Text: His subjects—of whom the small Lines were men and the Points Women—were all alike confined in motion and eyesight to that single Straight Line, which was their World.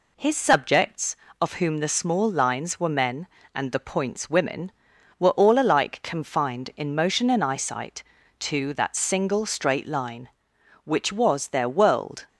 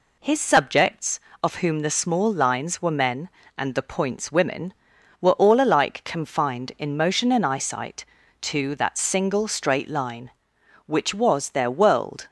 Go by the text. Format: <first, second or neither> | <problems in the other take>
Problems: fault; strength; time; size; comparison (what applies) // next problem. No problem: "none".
neither | none